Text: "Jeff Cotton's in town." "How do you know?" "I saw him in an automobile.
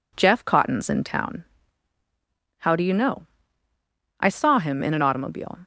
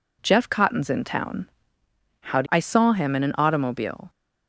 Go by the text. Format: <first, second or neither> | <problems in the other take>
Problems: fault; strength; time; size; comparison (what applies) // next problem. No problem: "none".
first | skips "you know"; at 2.4 s